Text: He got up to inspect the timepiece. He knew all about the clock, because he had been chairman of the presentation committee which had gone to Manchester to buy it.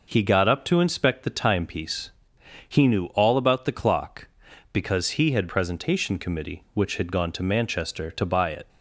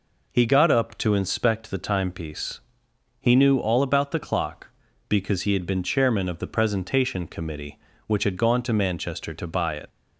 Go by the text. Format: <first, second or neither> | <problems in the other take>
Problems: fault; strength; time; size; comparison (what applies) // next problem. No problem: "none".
second | skips "been chairman of the"; at 5.4 s